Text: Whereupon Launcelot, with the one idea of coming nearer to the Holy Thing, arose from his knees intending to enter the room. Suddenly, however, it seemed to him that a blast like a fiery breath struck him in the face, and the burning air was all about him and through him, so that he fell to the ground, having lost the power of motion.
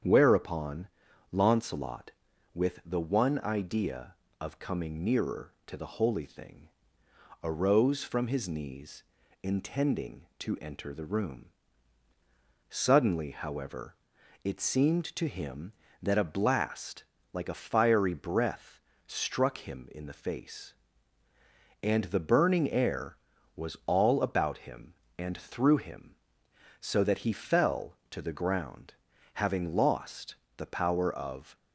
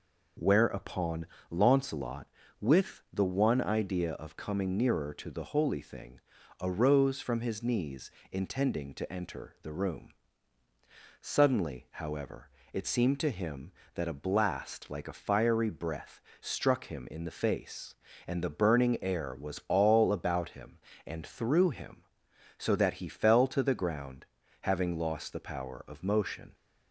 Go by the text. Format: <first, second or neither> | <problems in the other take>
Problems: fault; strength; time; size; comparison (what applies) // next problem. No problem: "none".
second | starts louder than the rest; strong; until 1.4 s; 8 dB // pauses between "Whereupon" and "Launcelot"; at 0.8 s; 0.42 s long; slight in the second // pauses between "knees" and "intending"; at 9.0 s; 0.38 s long; slight in the second // pauses between "blast" and "like"; slight; at 17.0 s; 0.26 s long // pauses between "breath" and "struck"; slight; at 18.8 s; 0.26 s long; slight in the second // pauses between "lost" and "the"; slight; at 30.3 s; 0.22 s long // stops before "motion"; at 31.5 s